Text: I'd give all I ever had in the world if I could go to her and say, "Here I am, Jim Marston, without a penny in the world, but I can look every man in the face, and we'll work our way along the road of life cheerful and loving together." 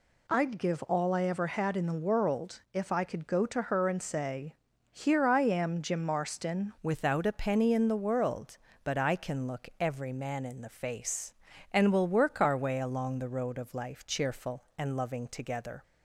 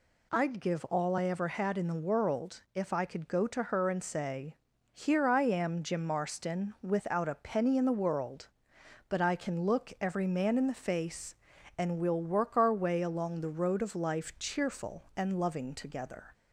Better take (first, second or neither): second